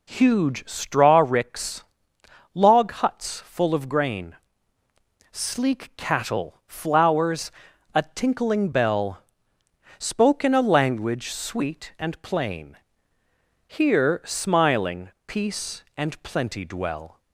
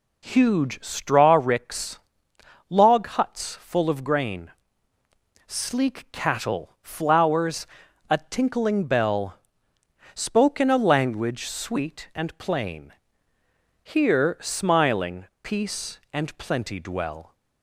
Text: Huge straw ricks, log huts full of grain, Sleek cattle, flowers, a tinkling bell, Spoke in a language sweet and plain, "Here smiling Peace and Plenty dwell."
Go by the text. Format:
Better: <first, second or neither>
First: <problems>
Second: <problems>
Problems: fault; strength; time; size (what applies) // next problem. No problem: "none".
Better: neither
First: pauses between "smiling" and "Peace"; slight; at 15.0 s; 0.16 s long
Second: pauses between "smiling" and "Peace"; slight; at 15.2 s; 0.16 s long